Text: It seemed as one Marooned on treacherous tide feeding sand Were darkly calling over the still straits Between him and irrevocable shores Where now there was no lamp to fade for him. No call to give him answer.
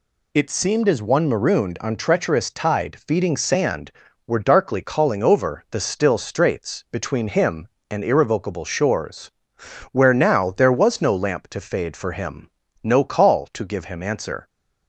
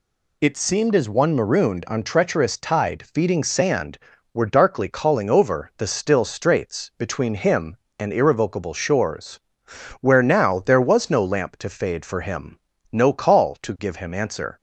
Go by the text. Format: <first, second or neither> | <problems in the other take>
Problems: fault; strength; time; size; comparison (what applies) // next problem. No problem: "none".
neither | pauses between "shores" and "Where"; noticeable; the same in both